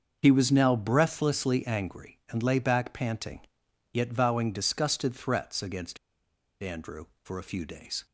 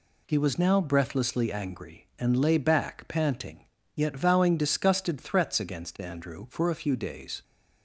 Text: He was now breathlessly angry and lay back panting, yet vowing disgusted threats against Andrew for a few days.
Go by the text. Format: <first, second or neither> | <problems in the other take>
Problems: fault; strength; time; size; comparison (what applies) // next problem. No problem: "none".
second | starts louder than the rest; until 1.2 s; 6.5 dB // pauses between "against" and "Andrew"; noticeable; at 5.9 s; 0.65 s long